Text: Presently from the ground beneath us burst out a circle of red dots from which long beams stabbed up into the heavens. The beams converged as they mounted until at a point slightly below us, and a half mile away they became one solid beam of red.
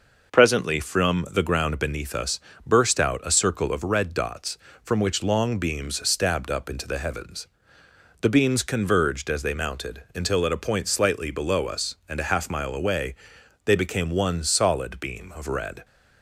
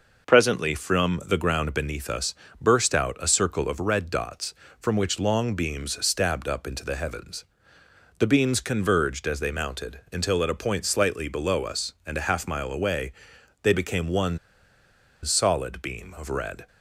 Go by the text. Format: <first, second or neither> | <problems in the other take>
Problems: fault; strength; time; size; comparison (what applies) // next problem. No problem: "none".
first | pauses between "us" and "burst"; slight; at 2.3 s; 0.24 s long; slight in the first // pauses between "away" and "they"; noticeable; at 13.1 s; 0.50 s long; noticeable in the first // pauses between "one" and "solid"; noticeable; at 14.3 s; 0.86 s long